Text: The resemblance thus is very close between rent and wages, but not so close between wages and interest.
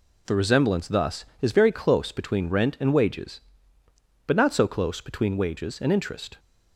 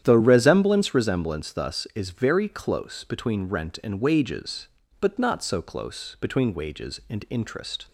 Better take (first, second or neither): first